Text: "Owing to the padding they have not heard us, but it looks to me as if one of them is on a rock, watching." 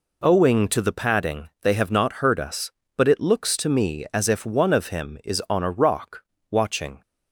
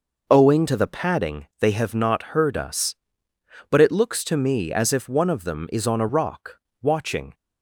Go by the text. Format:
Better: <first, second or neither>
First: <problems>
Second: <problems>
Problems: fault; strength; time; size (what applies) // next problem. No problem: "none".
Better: second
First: says "him" for "them"; at 4.8 s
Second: none